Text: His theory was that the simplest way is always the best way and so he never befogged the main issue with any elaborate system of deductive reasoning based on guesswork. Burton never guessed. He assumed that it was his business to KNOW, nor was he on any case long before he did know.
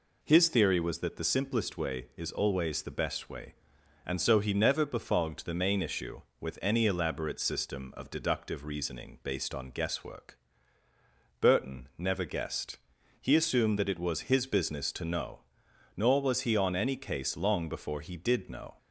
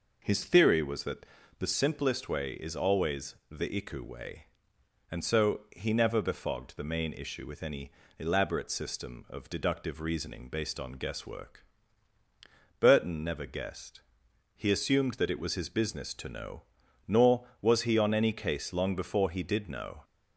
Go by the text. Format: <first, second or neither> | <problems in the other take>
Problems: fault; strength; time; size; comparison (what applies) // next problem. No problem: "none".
first | pauses between "that" and "the"; slight; at 1.2 s; 0.34 s long // pauses between "always" and "the"; slight; at 3.3 s; 0.16 s long // says "iku" for "best"; at 3.7 s // pauses between "any" and "elaborate"; slight; at 7.9 s; 0.26 s long